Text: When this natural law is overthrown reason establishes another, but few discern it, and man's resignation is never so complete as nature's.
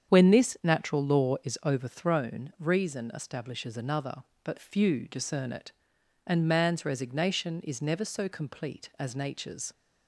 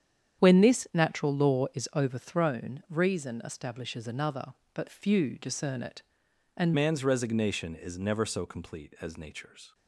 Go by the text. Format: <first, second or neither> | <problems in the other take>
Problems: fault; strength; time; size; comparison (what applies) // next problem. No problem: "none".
first | starts louder than the rest; strong; until 1.4 s; 8.5 dB; strong in the first // changes voice at "man's"; from 6.7 s on; 3.0 s long